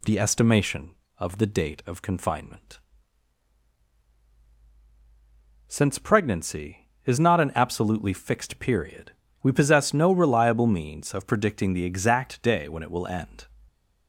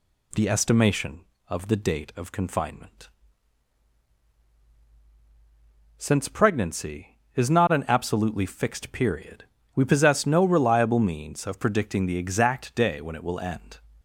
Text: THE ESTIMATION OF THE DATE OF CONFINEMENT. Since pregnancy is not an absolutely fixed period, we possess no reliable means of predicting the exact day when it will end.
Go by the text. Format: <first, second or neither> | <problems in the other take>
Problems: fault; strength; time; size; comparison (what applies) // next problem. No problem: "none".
neither | none